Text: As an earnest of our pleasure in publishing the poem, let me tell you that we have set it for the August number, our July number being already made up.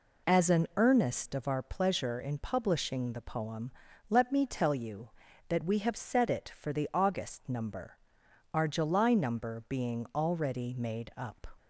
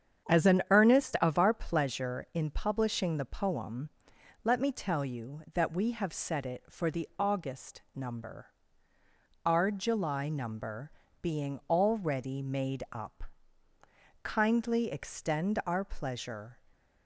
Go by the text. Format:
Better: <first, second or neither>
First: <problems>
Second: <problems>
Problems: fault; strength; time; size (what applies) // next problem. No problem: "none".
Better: first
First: none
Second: starts louder than the rest; strong; until 1.3 s; 8 dB // pauses between "number" and "being"; slight; at 10.9 s; 0.30 s long // goes on to say "Kindly extend our pleasure"; strong; from 14.2 s on; 2.3 s long